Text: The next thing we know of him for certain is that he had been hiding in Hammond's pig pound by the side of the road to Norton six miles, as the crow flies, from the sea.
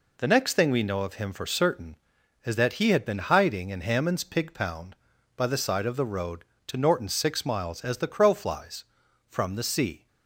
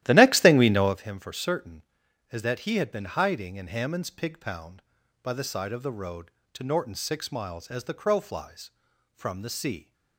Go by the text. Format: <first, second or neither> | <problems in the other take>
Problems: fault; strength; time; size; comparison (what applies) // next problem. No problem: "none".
first | starts louder than the rest; strong; until 1.0 s; 13.5 dB